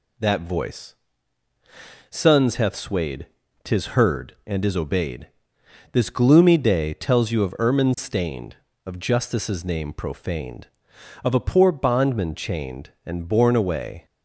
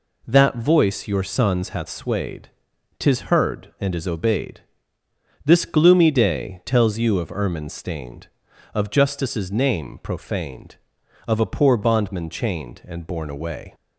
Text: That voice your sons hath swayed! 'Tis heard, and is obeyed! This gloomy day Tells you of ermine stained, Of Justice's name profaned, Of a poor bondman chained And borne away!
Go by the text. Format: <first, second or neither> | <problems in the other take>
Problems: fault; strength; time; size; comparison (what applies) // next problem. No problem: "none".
second | skips "your"; at 1.5 s